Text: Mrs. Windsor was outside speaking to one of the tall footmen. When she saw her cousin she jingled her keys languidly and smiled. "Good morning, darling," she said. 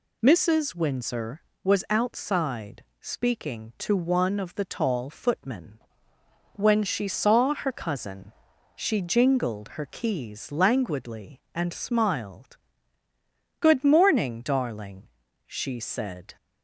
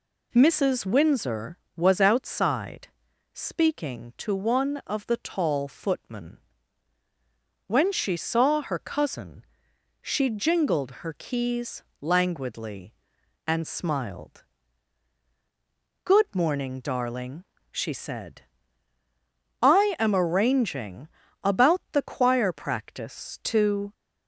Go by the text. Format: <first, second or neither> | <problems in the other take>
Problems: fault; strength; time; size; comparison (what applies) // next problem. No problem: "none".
first | pauses between "outside" and "speaking"; noticeable; at 2.8 s; 0.46 s long; slight in the first // pauses between "cousin" and "she"; noticeable; at 9.4 s; 0.58 s long; also in the first // pauses between "keys" and "languidly"; slight; at 11.8 s; 0.18 s long // goes on to say "I am arranging about the choir practice to"; strong; from 19.6 s on; 4.3 s long